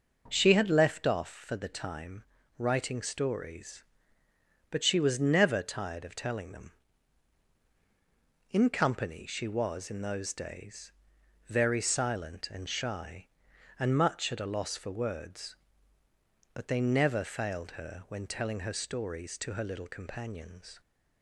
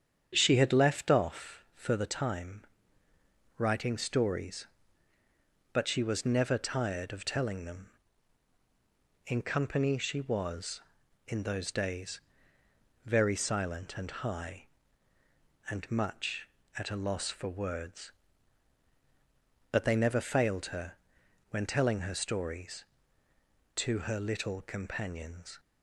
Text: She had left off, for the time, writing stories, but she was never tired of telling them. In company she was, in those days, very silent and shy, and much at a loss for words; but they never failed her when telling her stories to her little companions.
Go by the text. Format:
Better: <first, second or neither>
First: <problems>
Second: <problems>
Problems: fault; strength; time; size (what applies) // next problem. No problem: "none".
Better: first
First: none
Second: starts louder than the rest; strong; until 1.3 s; 8 dB // says "high" for "shy"; at 14.0 s // pauses between "her" and "when"; noticeable; at 20.9 s; 0.56 s long